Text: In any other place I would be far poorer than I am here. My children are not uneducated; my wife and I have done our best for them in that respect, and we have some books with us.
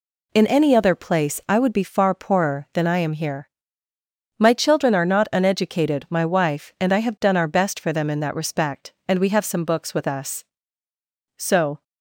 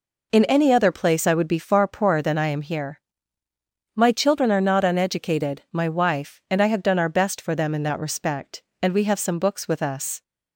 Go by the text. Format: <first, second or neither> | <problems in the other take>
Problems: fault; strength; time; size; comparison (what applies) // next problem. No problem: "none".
second | goes on to say "So"; slight; from 11.3 s on; 0.46 s long